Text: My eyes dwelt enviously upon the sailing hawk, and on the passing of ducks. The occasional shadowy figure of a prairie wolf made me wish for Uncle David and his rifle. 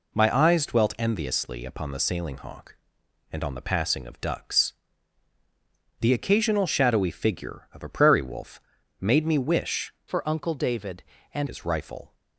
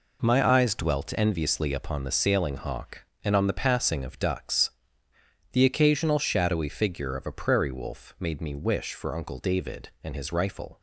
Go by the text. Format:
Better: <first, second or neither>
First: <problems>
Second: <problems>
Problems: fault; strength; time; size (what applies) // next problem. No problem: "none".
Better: second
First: pauses between "wolf" and "made"; at 8.6 s; 0.40 s long // changes voice from "for" to "and"; from 10.0 to 11.4 s; 1.4 s long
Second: none